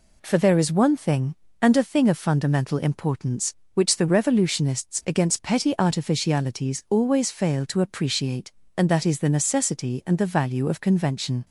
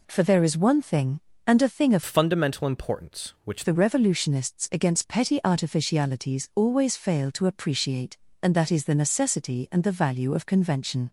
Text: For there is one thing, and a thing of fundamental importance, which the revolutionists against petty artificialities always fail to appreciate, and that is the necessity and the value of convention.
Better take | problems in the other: first | changes voice from "fundamental" to "which"; from 2.0 to 3.6 s; 1.6 s long

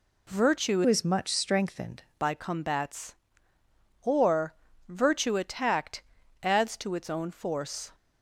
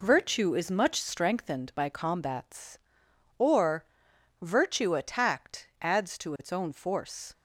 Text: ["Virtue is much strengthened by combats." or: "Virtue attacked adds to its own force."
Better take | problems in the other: second | changes voice from "is" to "strengthened"; from 0.8 to 2.0 s; 1.2 s long // pauses between "attacked" and "adds"; at 6.0 s; 0.38 s long

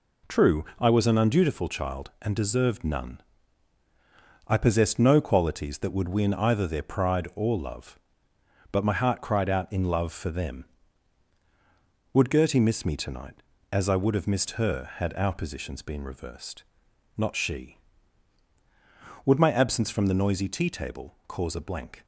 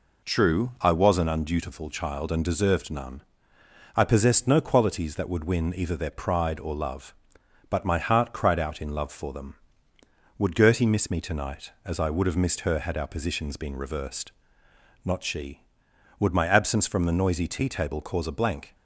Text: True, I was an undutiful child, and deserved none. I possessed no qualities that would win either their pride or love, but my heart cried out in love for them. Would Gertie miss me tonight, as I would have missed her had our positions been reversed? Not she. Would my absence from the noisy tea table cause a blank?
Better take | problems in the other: neither | none

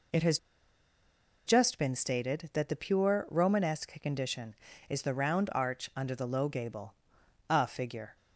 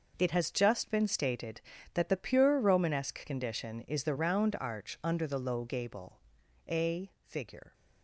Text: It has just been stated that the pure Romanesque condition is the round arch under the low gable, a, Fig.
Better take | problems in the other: second | pauses between "has" and "just"; at 0.3 s; 1.0 s long

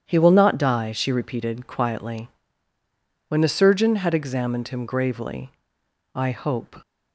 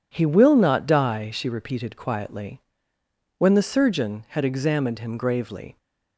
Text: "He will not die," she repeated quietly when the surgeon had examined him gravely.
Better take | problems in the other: second | starts louder than the rest; strong; until 1.0 s; 9 dB // pauses between "quietly" and "when"; at 2.2 s; 1.0 s long; noticeable in the second // goes on to say "I hope"; noticeable; from 6.1 s on; 0.62 s long

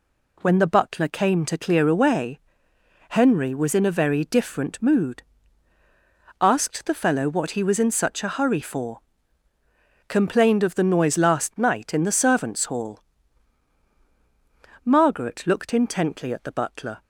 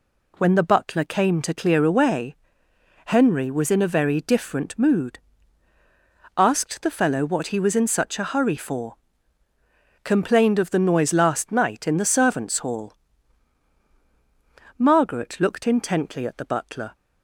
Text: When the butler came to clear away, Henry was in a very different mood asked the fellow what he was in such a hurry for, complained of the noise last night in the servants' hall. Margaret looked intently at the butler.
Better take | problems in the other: neither | pauses between "mood" and "asked"; the same in both

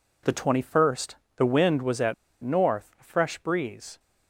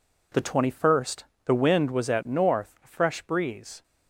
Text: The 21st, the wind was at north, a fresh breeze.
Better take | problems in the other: second | pauses between "at" and "north"; slight; at 2.1 s; 0.28 s long

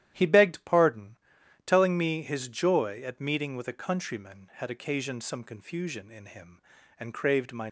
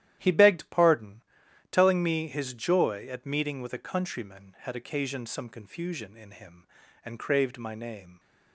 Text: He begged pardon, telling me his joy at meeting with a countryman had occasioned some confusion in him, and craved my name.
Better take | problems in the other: second | starts louder than the rest; strong; until 1.1 s; 12 dB; strong in the second // stops before "name"; at 7.6 s

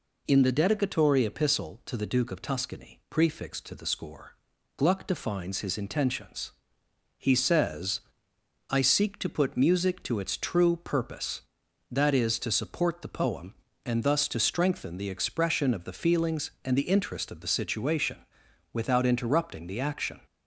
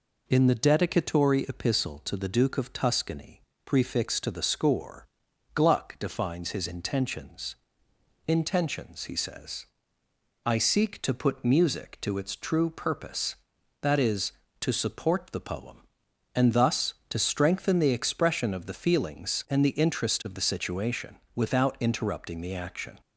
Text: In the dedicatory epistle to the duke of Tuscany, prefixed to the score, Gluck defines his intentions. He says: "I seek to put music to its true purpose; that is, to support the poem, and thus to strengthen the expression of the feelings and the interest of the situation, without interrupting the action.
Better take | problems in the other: first | says "intentions" twice; at 8.2 s

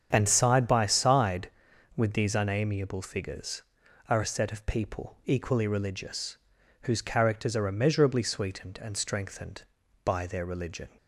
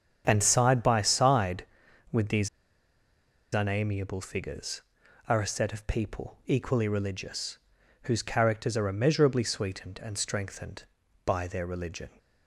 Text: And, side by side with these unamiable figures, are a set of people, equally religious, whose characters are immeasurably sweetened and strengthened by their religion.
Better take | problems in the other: first | starts louder than the rest; strong; until 1.2 s; 7.5 dB; strong in the first // pauses between "these" and "unamiable"; at 2.4 s; 1.0 s long

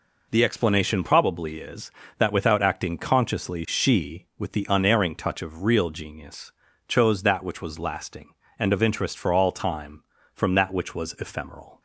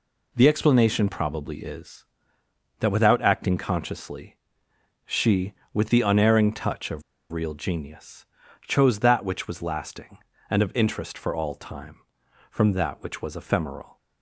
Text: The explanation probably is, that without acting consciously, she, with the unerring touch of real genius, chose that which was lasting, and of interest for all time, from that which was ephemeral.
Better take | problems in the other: first | pauses between "of" and "real"; slight; at 7.0 s; 0.29 s long

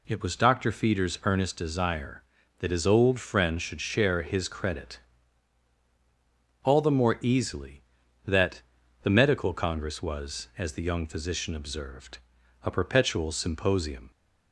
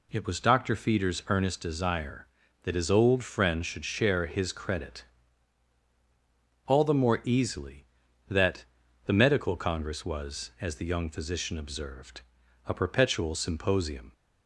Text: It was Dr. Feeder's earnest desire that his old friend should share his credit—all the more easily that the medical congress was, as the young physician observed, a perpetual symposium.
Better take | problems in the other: neither | pauses between "that" and "the"; the same in both

